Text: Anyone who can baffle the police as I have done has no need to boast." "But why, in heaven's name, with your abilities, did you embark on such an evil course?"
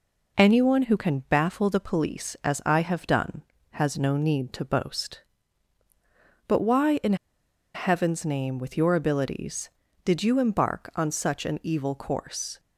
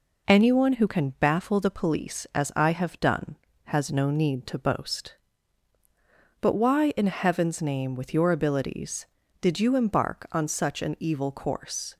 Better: second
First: pauses between "in" and "heaven's"; noticeable; at 7.1 s; 0.60 s long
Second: none

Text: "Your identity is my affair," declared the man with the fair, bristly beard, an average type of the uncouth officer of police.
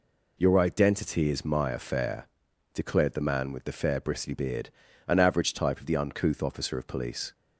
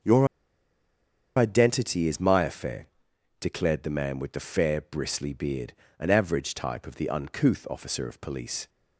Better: first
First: none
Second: starts louder than the rest; until 2.1 s; 6.5 dB // pauses between "Your" and "identity"; at 0.2 s; 1.1 s long

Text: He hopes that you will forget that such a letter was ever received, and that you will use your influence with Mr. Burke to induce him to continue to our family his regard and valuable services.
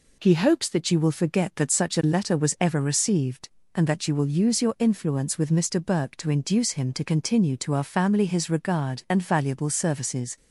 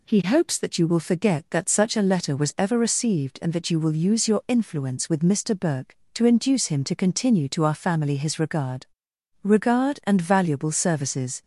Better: first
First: none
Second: says "regard" twice; at 9.4 s

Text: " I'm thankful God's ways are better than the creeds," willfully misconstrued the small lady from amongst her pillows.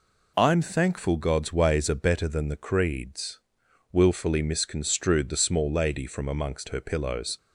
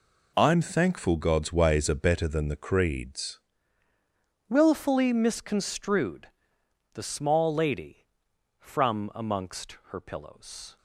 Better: first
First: none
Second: changes voice at "willfully"; from 4.4 s on; 6.3 s long // pauses between "misconstrued" and "the"; noticeable; at 6.2 s; 0.64 s long

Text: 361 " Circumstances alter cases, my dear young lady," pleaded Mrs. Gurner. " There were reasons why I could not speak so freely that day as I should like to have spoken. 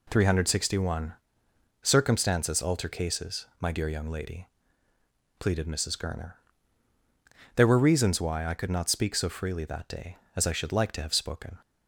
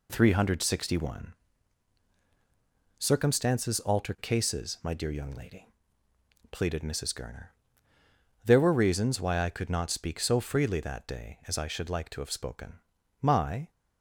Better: first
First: none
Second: goes on to say "My"; slight; from 13.2 s on; 0.48 s long

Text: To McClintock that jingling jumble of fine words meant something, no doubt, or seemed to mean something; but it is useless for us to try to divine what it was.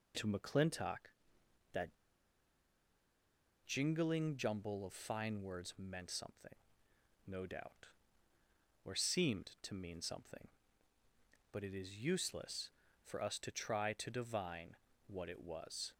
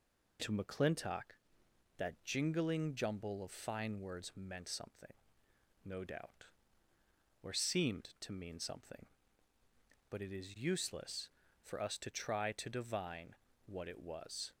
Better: second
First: pauses between "that" and "jingling"; strong; at 1.8 s; 1.7 s long // pauses between "divine" and "what"; slight; at 14.7 s; 0.30 s long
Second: pauses between "divine" and "what"; slight; at 13.3 s; 0.30 s long

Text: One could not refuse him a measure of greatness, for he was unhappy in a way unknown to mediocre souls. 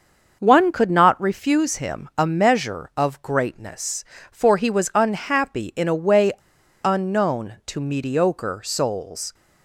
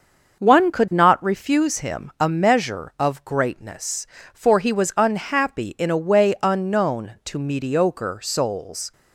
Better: second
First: starts louder than the rest; until 1.4 s; 6.5 dB // pauses between "way" and "unknown"; noticeable; at 6.3 s; 0.52 s long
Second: starts louder than the rest; until 1.4 s; 6.5 dB

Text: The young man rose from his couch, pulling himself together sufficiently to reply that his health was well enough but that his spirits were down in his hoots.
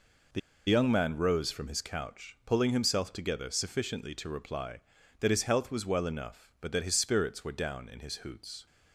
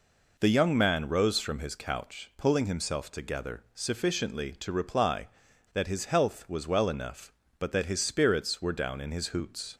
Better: second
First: pauses between "The" and "young"; slight; at 0.3 s; 0.29 s long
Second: none

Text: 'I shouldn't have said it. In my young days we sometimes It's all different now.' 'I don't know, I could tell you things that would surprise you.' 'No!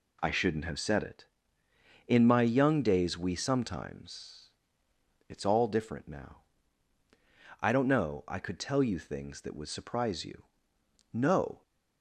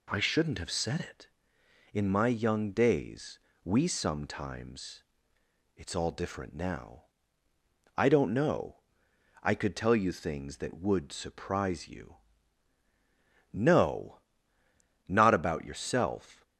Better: first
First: pauses between "sometimes" and "It's"; noticeable; at 4.4 s; 0.80 s long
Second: pauses between "days" and "we"; slight; at 3.3 s; 0.24 s long // pauses between "sometimes" and "It's"; noticeable; at 5.0 s; 0.74 s long // goes on to say "Not about yourself"; from 15.0 s on; 1.3 s long

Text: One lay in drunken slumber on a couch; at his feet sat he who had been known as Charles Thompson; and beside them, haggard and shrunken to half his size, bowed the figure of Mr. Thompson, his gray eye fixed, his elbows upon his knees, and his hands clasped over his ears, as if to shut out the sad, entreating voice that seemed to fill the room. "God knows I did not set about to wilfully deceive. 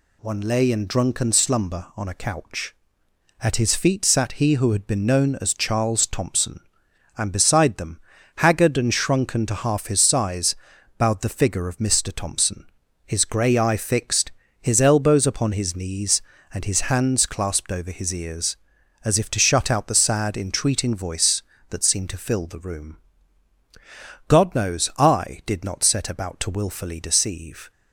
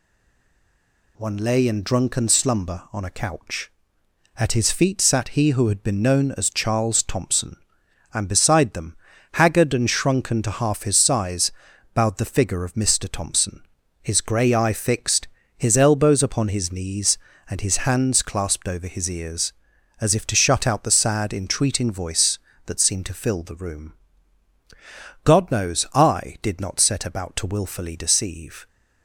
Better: first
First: none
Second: stays silent before the first word; noticeable; until 1.1 s; 1.1 s long

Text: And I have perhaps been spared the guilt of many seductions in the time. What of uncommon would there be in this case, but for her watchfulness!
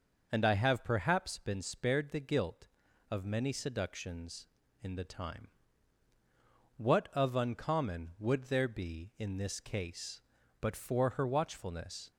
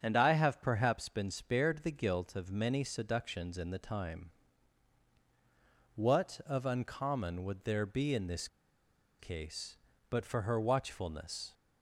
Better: first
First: starts louder than the rest; noticeable; until 1.3 s; 6 dB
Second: starts louder than the rest; strong; until 1.0 s; 7 dB // pauses between "this" and "case"; noticeable; at 8.4 s; 0.72 s long

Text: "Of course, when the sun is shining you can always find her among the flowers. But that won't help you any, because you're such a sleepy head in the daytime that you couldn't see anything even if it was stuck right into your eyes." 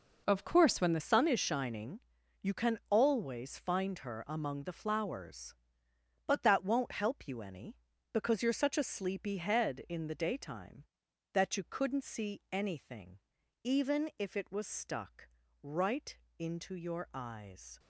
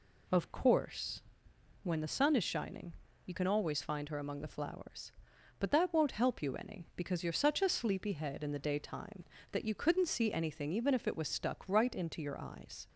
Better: second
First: changes voice at "sun"; from 0.9 s on; 16.8 s long // pauses between "shining" and "you"; at 2.0 s; 0.42 s long // pauses between "anything" and "even"; noticeable; at 13.1 s; 0.46 s long // pauses between "stuck" and "right"; slight; at 15.2 s; 0.34 s long // pauses between "right" and "into"; slight; at 16.1 s; 0.18 s long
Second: pauses between "shining" and "you"; slight; at 2.9 s; 0.32 s long

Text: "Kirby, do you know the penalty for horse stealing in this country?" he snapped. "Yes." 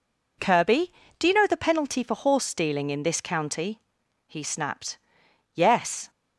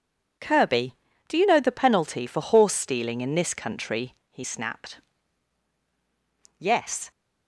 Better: second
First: says "county" for "country"; at 3.1 s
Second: none

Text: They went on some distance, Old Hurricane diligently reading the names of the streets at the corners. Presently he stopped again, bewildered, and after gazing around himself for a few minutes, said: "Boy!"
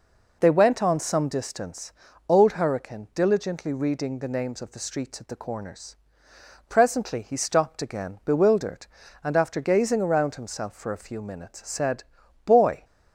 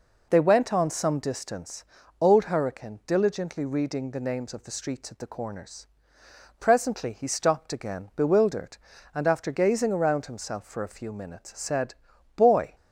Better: neither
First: none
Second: none

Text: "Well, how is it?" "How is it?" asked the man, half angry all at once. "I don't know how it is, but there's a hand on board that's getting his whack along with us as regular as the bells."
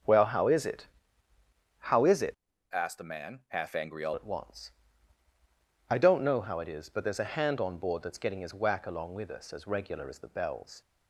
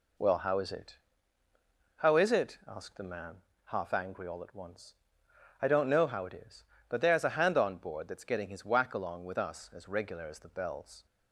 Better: second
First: starts louder than the rest; until 1.9 s; 6 dB // changes voice from "asked" to "all"; from 2.7 to 4.1 s; 1.4 s long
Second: none

